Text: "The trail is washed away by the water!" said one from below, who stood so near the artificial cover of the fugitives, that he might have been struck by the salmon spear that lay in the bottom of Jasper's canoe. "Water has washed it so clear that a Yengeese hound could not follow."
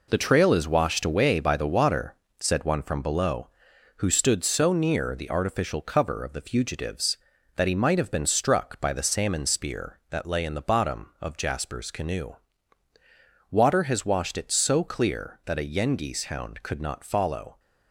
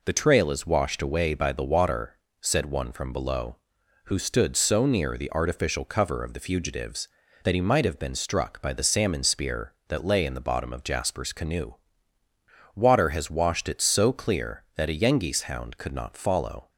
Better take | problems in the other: second | gets quieter; strong; throughout; 8 dB

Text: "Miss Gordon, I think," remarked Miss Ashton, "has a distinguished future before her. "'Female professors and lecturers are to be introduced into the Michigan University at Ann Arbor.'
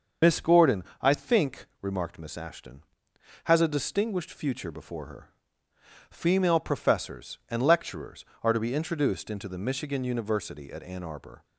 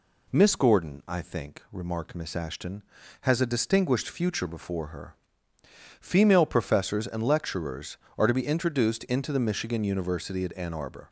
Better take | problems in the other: second | loses the start of "Miss"; at 0.2 s; 100 ms // starts louder than the rest; until 1.4 s; 6.5 dB

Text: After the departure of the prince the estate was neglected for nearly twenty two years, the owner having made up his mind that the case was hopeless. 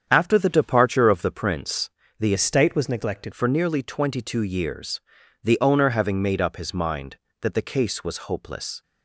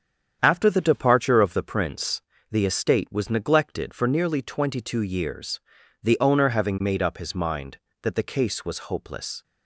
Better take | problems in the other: second | starts louder than the rest; strong; until 1.1 s; 8 dB; strong in the second // pauses between "prince" and "the"; slight; at 1.8 s; 0.28 s long; slight in the second // changes voice from "estate" to "neglected"; from 2.3 to 3.3 s; 1.0 s long

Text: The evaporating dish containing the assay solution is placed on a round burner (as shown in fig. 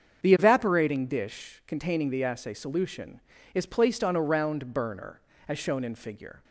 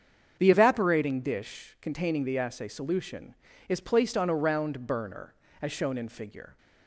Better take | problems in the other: neither | starts louder than the rest; strong; the same in both

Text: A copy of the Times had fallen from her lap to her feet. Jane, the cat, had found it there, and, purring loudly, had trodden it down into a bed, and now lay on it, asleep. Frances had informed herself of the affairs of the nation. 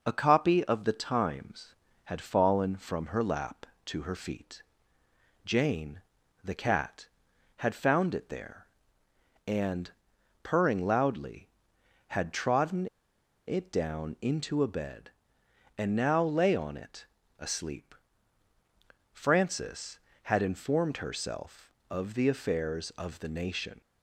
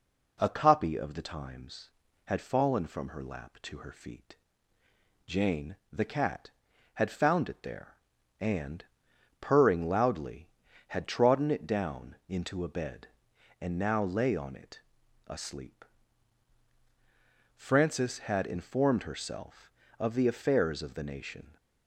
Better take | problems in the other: second | pauses between "trodden" and "it"; noticeable; at 12.8 s; 0.59 s long

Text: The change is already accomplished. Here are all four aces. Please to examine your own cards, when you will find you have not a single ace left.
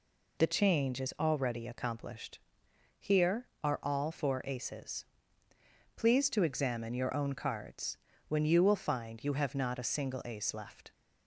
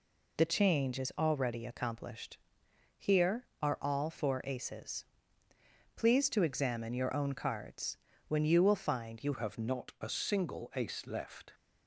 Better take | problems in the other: first | changes voice at "have"; from 9.3 s on; 2.2 s long

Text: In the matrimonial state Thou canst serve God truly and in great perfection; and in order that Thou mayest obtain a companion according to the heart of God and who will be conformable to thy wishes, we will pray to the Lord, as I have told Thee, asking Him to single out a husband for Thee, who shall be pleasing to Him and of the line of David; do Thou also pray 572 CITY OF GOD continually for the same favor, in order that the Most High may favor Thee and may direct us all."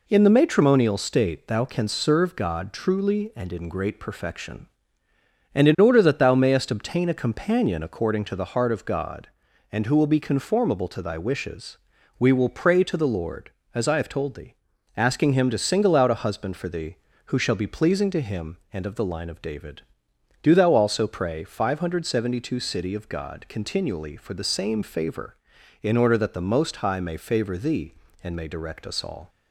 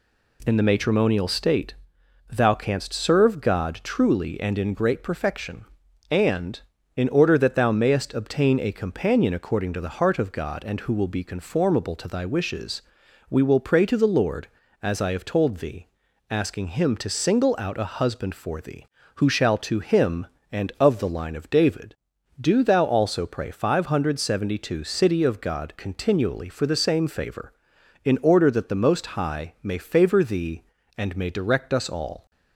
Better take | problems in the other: first | pauses between "state" and "Thou"; noticeable; at 1.7 s; 0.52 s long // skips "be pleasing"; at 19.5 s

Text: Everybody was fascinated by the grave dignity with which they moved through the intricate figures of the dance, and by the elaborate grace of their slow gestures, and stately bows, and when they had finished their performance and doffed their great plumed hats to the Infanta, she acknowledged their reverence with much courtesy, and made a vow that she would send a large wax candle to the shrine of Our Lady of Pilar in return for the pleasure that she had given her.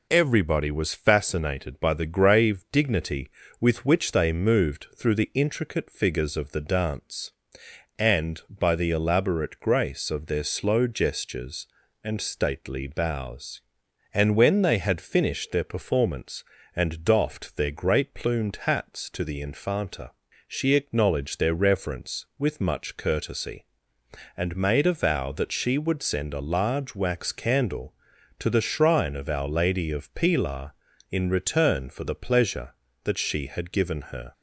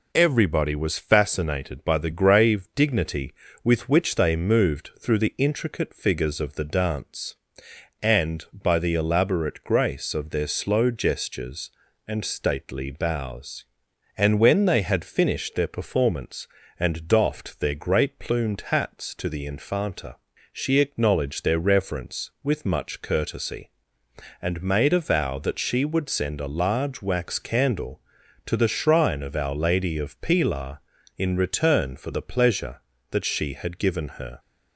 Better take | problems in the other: neither | none

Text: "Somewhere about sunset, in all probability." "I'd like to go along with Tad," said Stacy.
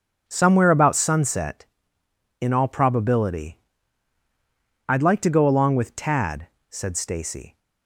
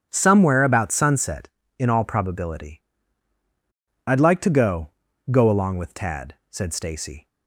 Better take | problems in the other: first | starts louder than the rest; strong; until 1.1 s; 8.5 dB; also in the first // says "go" twice; at 5.2 s

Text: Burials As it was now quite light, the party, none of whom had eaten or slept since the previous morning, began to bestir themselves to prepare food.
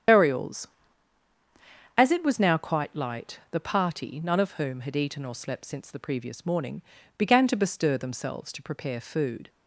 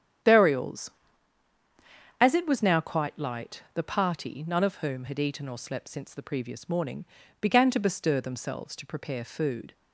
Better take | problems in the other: second | loses the start of "Burials"; at 0.0 s; 80 ms // starts louder than the rest; strong; until 2.4 s; 8.5 dB; strong in the second

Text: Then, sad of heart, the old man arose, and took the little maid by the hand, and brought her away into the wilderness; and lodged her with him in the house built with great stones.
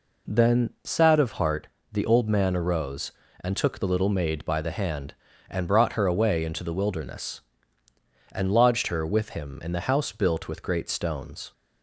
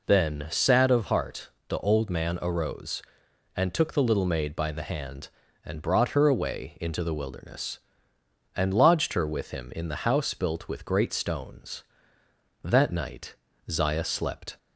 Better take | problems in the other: first | goes on to say "That night Zaya slept"; strong; from 12.6 s on; 1.9 s long

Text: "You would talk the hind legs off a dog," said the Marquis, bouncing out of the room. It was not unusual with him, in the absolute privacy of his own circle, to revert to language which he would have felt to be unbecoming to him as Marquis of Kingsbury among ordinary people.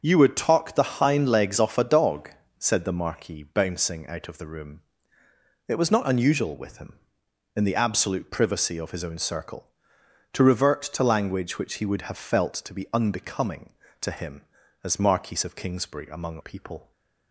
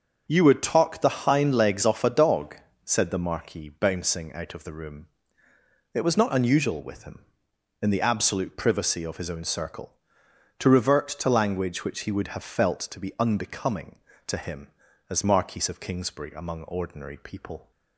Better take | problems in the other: second | starts louder than the rest; until 1.0 s; 6.5 dB; also in the second // skips "ordinary"; at 16.4 s

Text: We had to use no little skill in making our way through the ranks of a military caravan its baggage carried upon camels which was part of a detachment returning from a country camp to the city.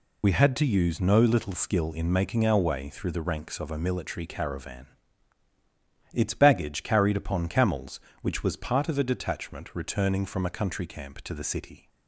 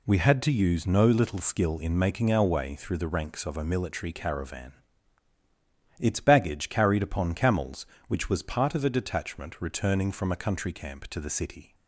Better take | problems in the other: second | loses the start of "We"; at 0.2 s; 40 ms // pauses between "caravan" and "its"; strong; at 4.8 s; 1.2 s long; strong in the second

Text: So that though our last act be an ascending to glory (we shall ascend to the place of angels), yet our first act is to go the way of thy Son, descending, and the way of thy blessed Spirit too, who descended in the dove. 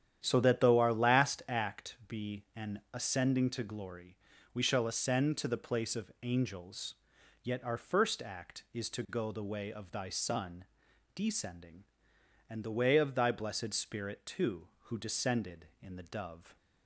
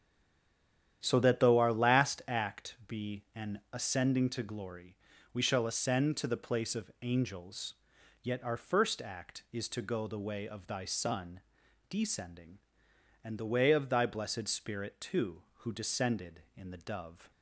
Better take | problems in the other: first | stays silent before the first word; until 1.0 s; 1.0 s long // starts louder than the rest; strong; until 2.0 s; 10 dB; strong in the first

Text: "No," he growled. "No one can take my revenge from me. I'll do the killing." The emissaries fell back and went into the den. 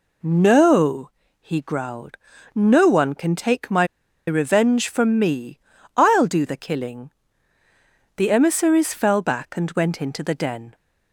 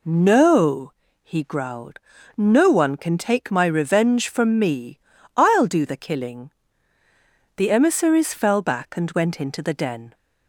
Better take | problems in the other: second | pauses between "my" and "revenge"; at 3.8 s; 0.43 s long

